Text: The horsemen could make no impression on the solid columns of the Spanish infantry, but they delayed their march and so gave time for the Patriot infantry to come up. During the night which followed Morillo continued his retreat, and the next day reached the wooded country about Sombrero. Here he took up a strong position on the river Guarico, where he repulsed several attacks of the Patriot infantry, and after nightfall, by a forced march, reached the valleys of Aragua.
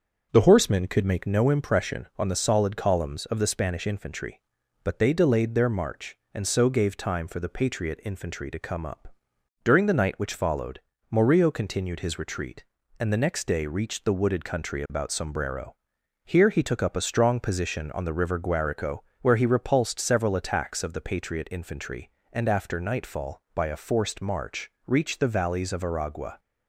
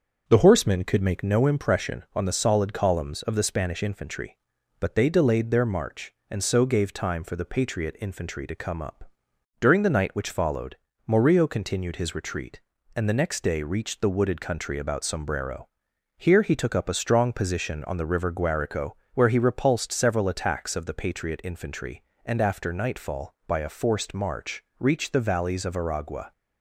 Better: neither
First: starts louder than the rest; until 1.3 s; 6.5 dB // pauses between "followed" and "Morillo"; slight; at 10.8 s; 0.30 s long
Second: starts louder than the rest; until 1.2 s; 6.5 dB // pauses between "followed" and "Morillo"; slight; at 10.7 s; 0.30 s long

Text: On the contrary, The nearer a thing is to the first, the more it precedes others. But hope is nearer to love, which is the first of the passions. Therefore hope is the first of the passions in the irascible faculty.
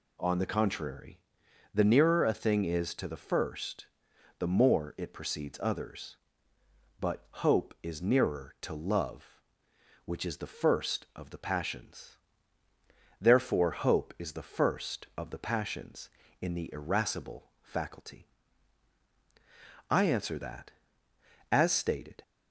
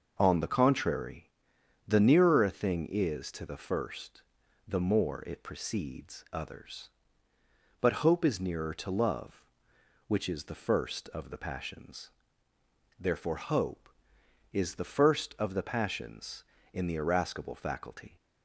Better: second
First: pauses between "But" and "hope"; slight; at 7.2 s; 0.16 s long // goes on to say "I answer that As stated"; strong; from 19.9 s on; 2.3 s long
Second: none

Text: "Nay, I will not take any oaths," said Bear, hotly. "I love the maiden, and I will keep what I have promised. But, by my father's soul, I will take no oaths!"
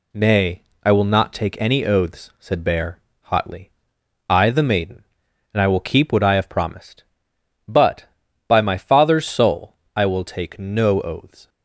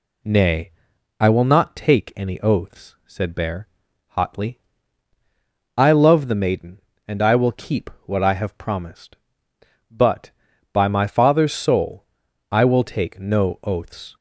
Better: second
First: skips "love"; at 4.4 s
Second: none

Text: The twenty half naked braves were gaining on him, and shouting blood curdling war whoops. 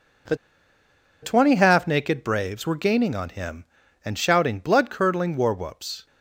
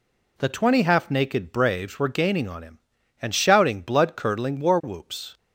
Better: second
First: pauses between "The" and "twenty"; noticeable; at 0.3 s; 0.88 s long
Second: none

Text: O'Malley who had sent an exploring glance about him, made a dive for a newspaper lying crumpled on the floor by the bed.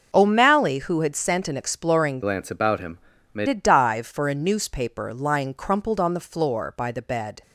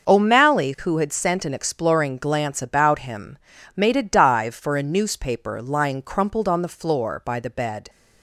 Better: second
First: changes voice from "glance" to "made"; from 2.2 to 3.4 s; 1.2 s long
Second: none

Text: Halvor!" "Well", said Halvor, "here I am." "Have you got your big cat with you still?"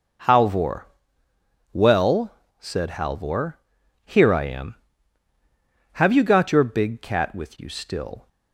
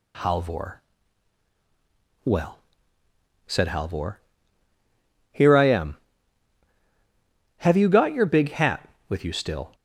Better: first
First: none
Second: says "hat" for "cat"; at 8.5 s

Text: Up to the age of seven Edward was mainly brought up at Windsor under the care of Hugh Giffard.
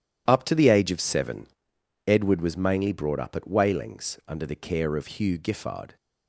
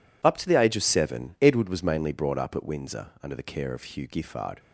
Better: second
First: pauses between "seven" and "Edward"; noticeable; at 1.4 s; 0.62 s long // says "Wailings" for "Windsor"; at 3.4 s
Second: none

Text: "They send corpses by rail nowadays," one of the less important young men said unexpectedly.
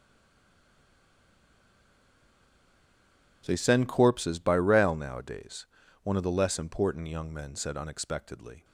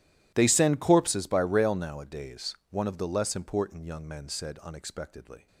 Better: second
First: stays silent before the first word; strong; until 3.4 s; 3.4 s long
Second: none

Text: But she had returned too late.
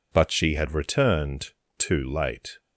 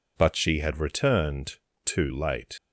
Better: first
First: pauses between "returned" and "too"; slight; at 1.5 s; 0.26 s long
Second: pauses between "returned" and "too"; slight; at 1.5 s; 0.28 s long // leaves "late" unfinished; at 2.5 s; 70 ms

